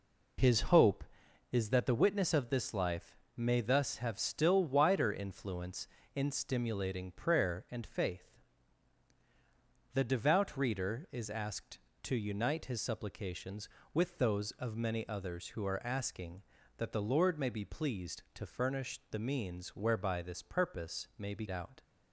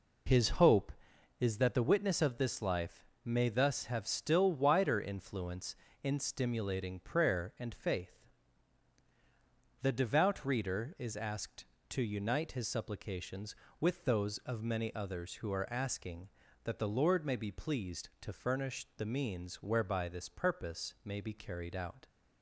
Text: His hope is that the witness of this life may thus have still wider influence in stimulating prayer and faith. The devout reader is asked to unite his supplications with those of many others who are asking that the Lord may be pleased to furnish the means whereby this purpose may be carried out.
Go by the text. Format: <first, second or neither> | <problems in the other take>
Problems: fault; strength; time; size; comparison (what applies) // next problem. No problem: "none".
second | pauses between "life" and "may"; slight; at 3.1 s; 0.18 s long; slight in the second // skips "carried"; at 21.4 s